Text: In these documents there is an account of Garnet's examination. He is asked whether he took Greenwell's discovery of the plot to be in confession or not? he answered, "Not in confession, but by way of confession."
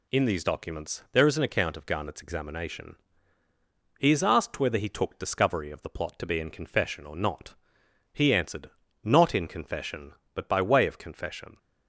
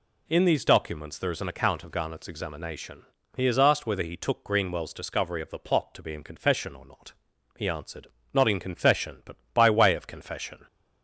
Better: second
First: skips "Greenwell's"; at 5.1 s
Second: none

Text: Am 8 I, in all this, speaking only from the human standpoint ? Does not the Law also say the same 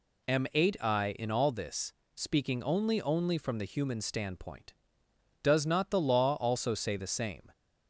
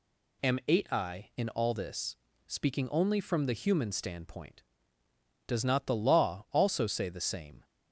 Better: second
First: says "only" twice; at 3.0 s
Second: none

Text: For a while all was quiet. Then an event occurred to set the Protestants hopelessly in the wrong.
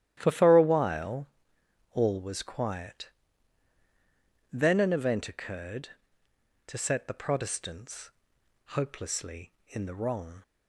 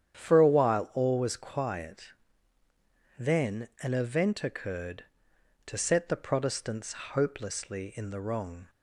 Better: second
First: starts louder than the rest; strong; until 1.1 s; 12 dB // says "For" twice; at 0.3 s // pauses between "while" and "all"; noticeable; at 1.2 s; 0.64 s long // pauses between "Protestants" and "hopelessly"; noticeable; at 8.1 s; 0.56 s long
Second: starts louder than the rest; strong; until 1.2 s; 9 dB // pauses between "Protestants" and "hopelessly"; slight; at 6.9 s; 0.20 s long

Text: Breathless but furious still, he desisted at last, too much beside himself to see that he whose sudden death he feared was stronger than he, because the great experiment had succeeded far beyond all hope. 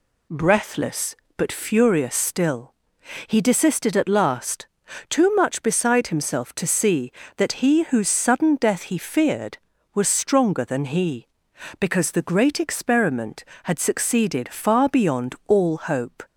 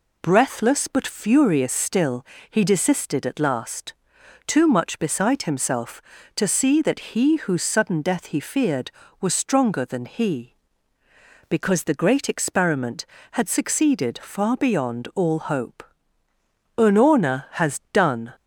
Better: first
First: none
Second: goes on to say "Unorna has done"; from 16.7 s on; 1.5 s long

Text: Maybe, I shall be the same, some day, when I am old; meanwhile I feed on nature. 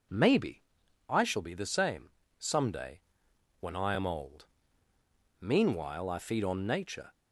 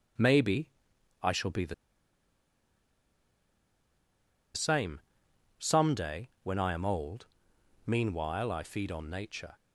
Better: first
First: none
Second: pauses between "the" and "same"; strong; at 1.7 s; 2.8 s long

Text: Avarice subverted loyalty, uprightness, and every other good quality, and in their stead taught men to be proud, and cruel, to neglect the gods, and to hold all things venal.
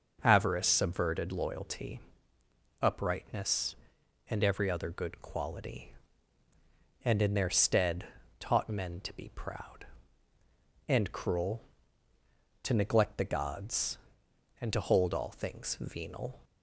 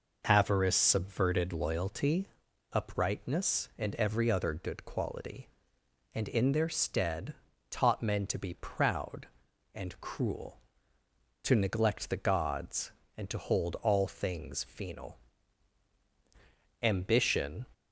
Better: first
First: pauses between "stead" and "taught"; slight; at 8.0 s; 0.34 s long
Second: pauses between "stead" and "taught"; at 7.3 s; 0.38 s long // goes on to say "Ambition"; noticeable; from 16.8 s on; 0.82 s long

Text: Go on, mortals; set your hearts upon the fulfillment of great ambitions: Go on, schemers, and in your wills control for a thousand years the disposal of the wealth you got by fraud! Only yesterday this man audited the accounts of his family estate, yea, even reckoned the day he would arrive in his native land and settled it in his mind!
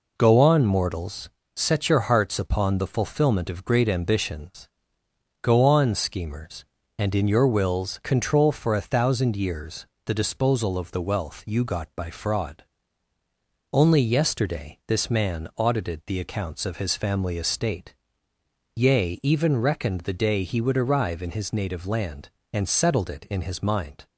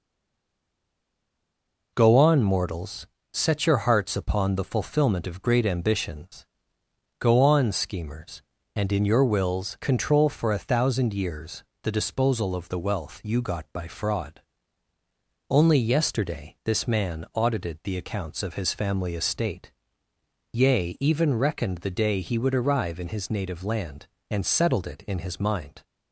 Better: first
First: pauses between "years" and "the"; slight; at 9.8 s; 0.20 s long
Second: stays silent before the first word; noticeable; until 1.9 s; 1.9 s long // pauses between "years" and "the"; slight; at 11.6 s; 0.20 s long

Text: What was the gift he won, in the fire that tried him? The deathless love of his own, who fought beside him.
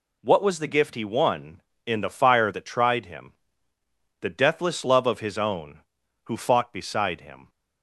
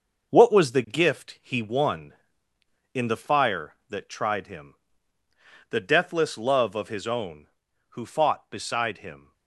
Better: first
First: none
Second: gets quieter; strong; throughout; 7 dB

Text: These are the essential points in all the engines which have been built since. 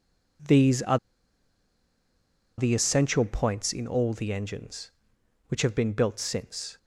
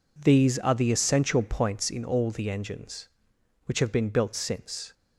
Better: second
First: pauses between "are" and "the"; strong; at 0.9 s; 1.6 s long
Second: none

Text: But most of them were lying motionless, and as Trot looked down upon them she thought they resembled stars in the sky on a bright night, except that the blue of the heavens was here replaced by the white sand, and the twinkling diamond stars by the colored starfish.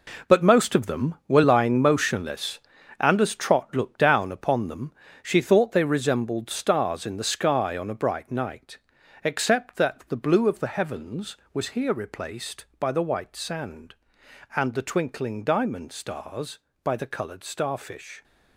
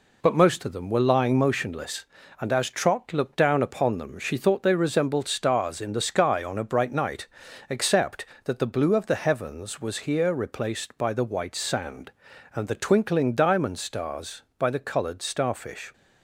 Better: second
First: gets quieter; strong; throughout; 9.5 dB // pauses between "them" and "she"; slight; at 4.9 s; 0.28 s long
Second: none

